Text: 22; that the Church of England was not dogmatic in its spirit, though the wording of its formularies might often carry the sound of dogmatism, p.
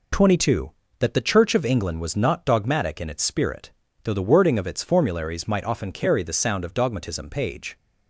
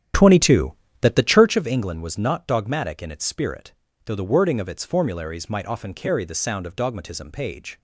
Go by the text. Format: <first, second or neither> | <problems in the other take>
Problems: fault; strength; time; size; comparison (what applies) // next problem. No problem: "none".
first | starts louder than the rest; strong; until 1.6 s; 10 dB